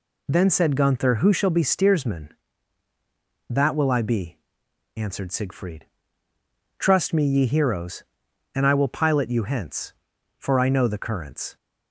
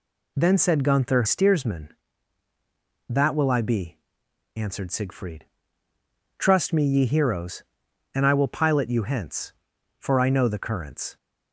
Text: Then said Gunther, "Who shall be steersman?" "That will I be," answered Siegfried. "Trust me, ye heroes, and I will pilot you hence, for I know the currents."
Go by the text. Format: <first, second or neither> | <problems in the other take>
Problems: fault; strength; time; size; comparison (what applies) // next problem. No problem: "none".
first | skips "Who shall be"; at 1.2 s